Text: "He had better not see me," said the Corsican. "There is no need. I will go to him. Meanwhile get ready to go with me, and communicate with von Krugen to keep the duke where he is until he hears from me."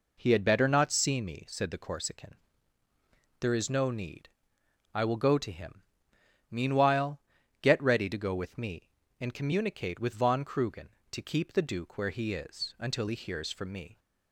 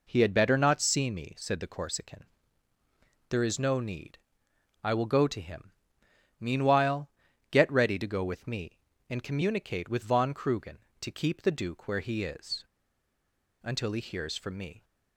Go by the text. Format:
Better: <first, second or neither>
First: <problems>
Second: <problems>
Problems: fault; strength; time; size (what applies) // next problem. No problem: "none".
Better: first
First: pauses between "Meanwhile" and "get"; at 7.2 s; 0.40 s long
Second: pauses between "Meanwhile" and "get"; at 7.0 s; 0.40 s long // pauses between "is" and "until"; at 12.6 s; 1.0 s long